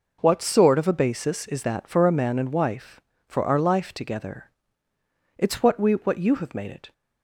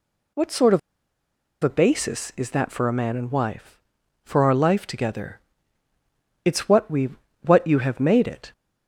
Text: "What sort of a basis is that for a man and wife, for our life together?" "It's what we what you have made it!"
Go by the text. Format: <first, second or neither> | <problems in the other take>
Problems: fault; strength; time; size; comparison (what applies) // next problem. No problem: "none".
first | pauses between "of" and "a"; noticeable; at 0.7 s; 0.84 s long // pauses between "we" and "what"; slight; at 7.0 s; 0.32 s long